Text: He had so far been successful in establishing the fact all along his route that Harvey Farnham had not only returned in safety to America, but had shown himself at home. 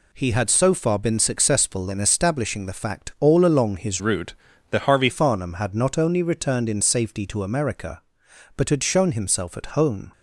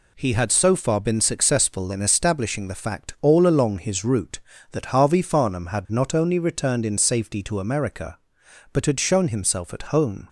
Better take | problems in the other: second | changes voice from "route" to "Harvey"; from 3.9 to 5.0 s; 1.1 s long

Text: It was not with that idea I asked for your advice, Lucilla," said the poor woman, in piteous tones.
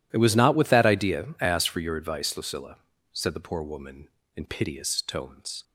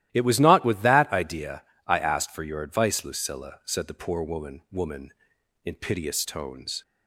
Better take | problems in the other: first | starts louder than the rest; strong; until 1.1 s; 14 dB // pauses between "idea" and "I"; slight; at 1.6 s; 0.24 s long // says "woman" twice; at 4.7 s

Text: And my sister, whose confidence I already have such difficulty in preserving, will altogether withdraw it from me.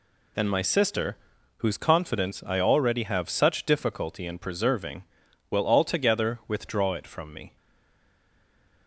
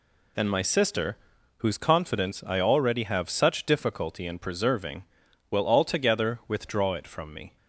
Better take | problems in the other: second | stays silent after the last word; noticeable; from 7.5 s on; 1.3 s long

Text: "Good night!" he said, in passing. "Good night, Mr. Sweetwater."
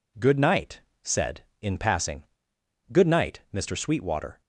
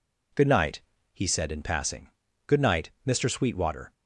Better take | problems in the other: second | skips "he"; at 0.9 s

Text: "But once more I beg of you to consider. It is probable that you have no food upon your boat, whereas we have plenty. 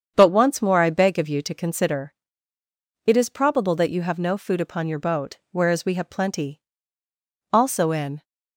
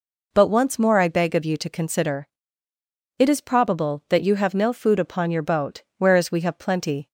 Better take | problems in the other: second | starts louder than the rest; strong; until 1.1 s; 7.5 dB // goes on to say "Also in"; noticeable; from 7.5 s on; 0.72 s long

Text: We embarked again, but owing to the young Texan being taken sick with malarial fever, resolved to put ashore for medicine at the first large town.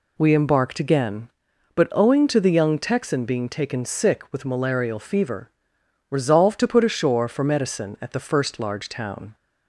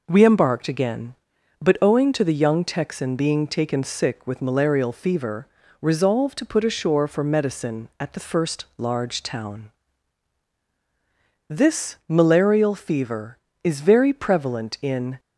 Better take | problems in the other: first | goes on to say "This malarial fever is very prevalent in"; strong; from 11.4 s on; 3.7 s long

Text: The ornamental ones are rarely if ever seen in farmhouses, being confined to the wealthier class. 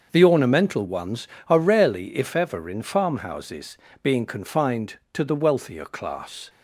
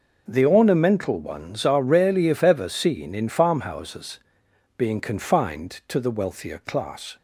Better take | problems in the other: second | starts louder than the rest; until 1.1 s; 6 dB // skips "seen"; at 2.6 s

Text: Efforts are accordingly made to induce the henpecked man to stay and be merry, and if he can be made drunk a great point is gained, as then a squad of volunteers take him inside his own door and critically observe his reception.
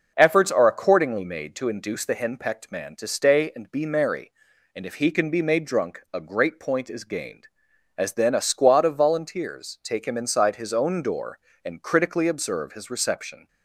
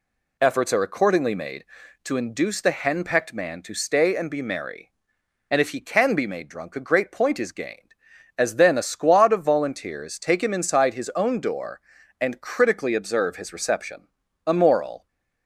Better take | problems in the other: first | goes on to say "A moral"; noticeable; from 14.4 s on; 0.62 s long

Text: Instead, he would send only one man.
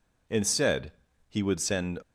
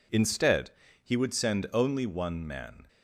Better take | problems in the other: second | stops before "only one man"; at 2.0 s

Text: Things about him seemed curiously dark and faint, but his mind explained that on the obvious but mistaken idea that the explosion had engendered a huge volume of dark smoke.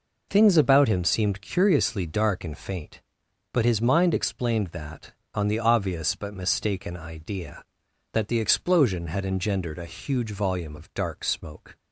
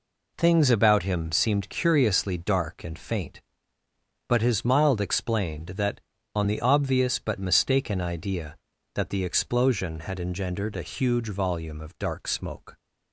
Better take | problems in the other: first | says "mild" for "mind"; at 4.6 s

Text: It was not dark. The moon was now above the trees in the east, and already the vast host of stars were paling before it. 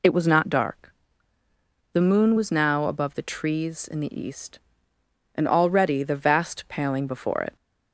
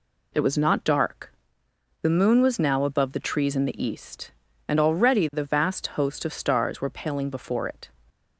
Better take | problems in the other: second | skips "host of stars were"; at 6.6 s

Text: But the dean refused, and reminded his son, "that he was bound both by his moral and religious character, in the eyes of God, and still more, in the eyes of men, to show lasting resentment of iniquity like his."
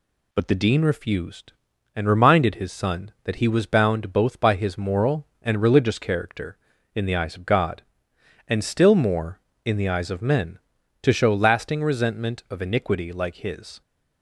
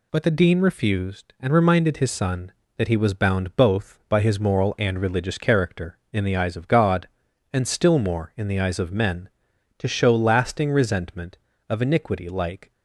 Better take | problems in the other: first | stops before "his"; at 12.7 s

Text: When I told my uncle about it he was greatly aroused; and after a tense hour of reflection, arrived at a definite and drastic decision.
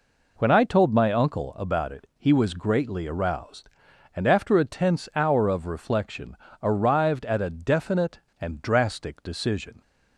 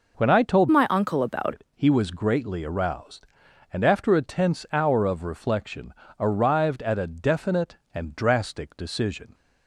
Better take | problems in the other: first | changes voice from "my" to "about"; from 0.7 to 1.5 s; 0.8 s long

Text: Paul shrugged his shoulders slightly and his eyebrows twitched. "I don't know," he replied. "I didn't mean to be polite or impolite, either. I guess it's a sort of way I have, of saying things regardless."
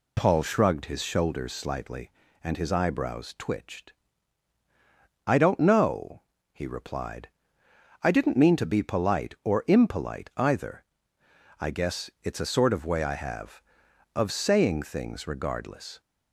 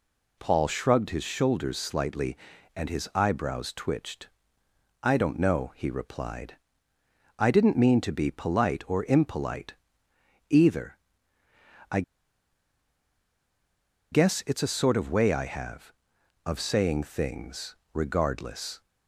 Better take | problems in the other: first | pauses between "I" and "guess"; strong; at 12.0 s; 2.1 s long // pauses between "things" and "regardless"; slight; at 17.7 s; 0.16 s long

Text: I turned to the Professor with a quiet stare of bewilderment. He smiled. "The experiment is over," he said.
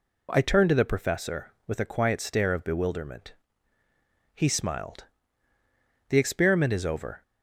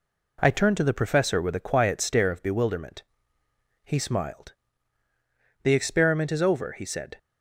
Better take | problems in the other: second | stops before "he said"; at 7.2 s

